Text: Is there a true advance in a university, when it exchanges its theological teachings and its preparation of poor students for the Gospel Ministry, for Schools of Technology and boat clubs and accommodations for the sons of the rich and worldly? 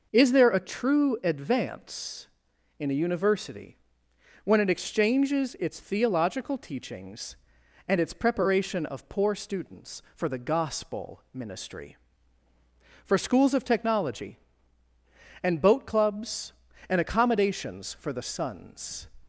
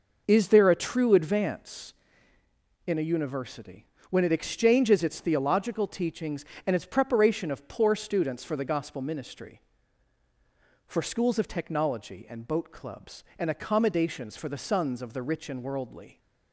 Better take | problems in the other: second | stops before "of the rich and worldly"; at 19.2 s

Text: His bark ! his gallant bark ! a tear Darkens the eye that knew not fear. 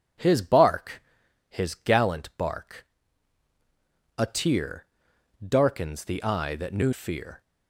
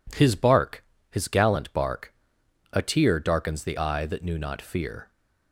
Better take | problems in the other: second | pauses between "tear" and "Darkens"; noticeable; at 4.8 s; 0.56 s long // skips "not"; at 6.9 s

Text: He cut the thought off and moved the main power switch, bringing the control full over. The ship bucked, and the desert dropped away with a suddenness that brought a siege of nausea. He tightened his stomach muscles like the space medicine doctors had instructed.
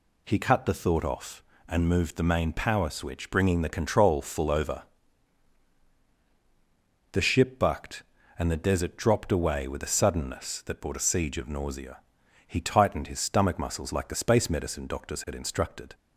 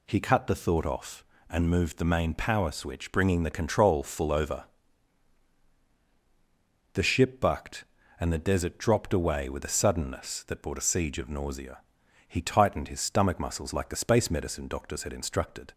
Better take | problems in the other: neither | none

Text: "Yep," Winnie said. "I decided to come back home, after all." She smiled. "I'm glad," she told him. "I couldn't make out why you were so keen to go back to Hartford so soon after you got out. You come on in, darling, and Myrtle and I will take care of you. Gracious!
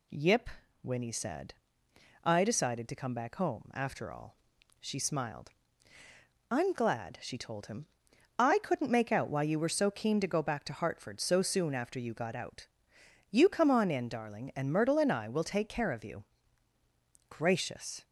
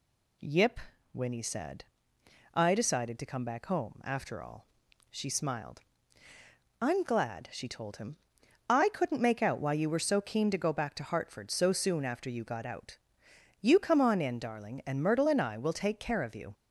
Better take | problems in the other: first | stops before "Gracious"; at 16.5 s

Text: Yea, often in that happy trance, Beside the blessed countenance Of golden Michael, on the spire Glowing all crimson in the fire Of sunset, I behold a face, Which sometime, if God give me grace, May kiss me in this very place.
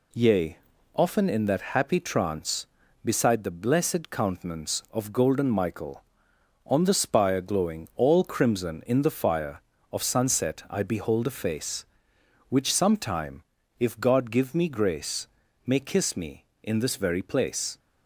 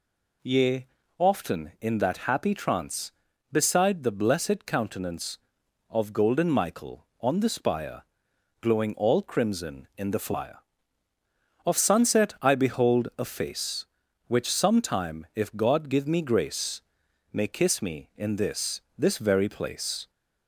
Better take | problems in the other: first | pauses between "spire" and "Glowing"; noticeable; at 8.0 s; 0.58 s long // says "this" twice; at 18.9 s

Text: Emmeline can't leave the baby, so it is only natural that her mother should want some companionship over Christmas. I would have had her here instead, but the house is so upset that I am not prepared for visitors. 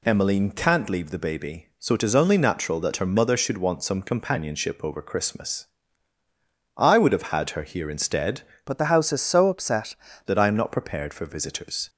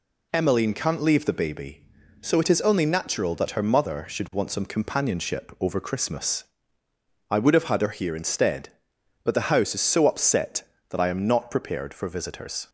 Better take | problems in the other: second | changes voice from "but" to "upset"; from 8.6 to 9.9 s; 1.3 s long

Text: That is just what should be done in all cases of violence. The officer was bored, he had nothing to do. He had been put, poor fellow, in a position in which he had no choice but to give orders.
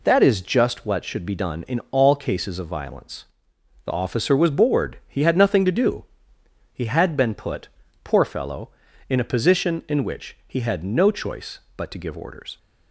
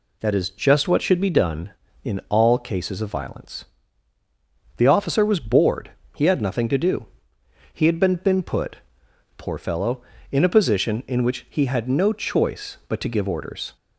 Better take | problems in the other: first | says "been" twice; at 8.1 s

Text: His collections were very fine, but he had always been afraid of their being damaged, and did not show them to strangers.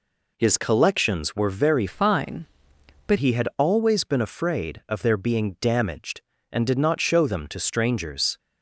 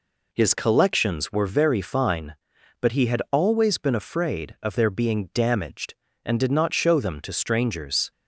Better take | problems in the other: second | changes voice from "fine" to "but"; from 1.8 to 3.1 s; 1.3 s long

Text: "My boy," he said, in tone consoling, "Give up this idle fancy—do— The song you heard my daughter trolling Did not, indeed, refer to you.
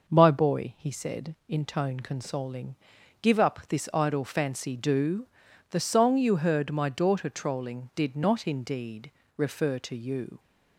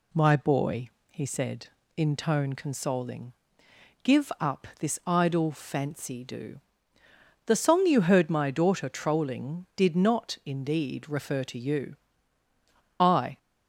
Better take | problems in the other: first | goes on to say "I"; slight; from 12.9 s on; 0.38 s long

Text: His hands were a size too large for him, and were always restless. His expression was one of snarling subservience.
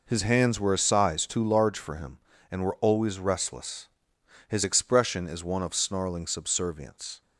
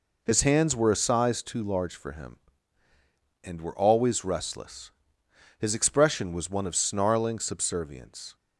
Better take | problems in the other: second | says "is" for "was"; at 5.2 s

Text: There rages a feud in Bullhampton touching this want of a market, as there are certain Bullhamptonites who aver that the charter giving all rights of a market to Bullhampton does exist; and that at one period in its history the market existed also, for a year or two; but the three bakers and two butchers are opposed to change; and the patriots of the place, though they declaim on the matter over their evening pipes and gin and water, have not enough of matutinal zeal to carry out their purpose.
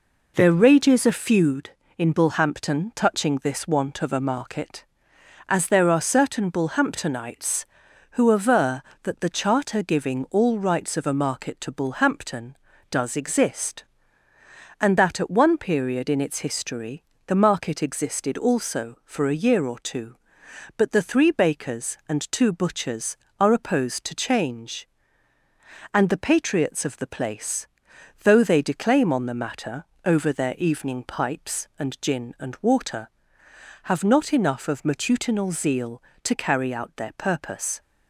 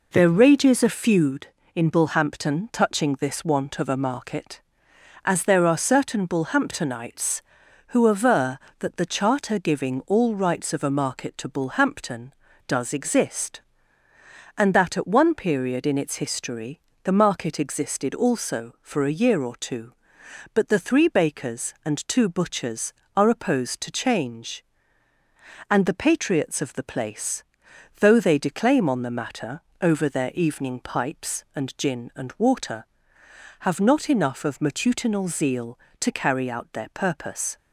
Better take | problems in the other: neither | pauses between "history" and "the"; slight; the same in both // pauses between "matter" and "over"; slight; the same in both

